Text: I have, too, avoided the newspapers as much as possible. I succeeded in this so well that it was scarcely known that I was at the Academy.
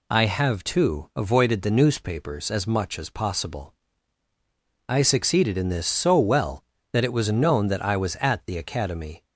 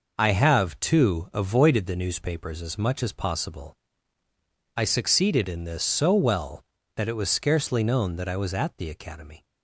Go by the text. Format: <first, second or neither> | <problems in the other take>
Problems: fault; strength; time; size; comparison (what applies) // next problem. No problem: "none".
second | skips "scarcely"; at 7.3 s